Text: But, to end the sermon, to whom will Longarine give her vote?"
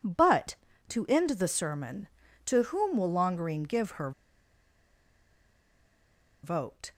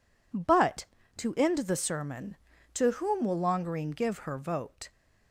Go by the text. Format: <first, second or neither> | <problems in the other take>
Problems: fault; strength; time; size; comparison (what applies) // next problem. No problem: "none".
second | pauses between "her" and "vote"; strong; at 4.1 s; 2.3 s long